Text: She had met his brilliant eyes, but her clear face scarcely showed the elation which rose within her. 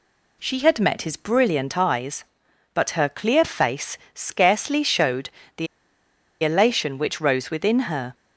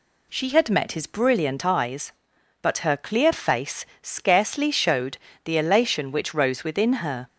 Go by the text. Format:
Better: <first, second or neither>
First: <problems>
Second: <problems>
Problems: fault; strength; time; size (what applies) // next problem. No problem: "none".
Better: second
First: pauses between "face" and "scarcely"; slight; at 3.9 s; 0.16 s long // pauses between "showed" and "the"; slight; at 5.2 s; 0.28 s long // pauses between "the" and "elation"; noticeable; at 5.6 s; 0.77 s long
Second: pauses between "face" and "scarcely"; slight; at 3.8 s; 0.16 s long // pauses between "showed" and "the"; slight; at 5.1 s; 0.28 s long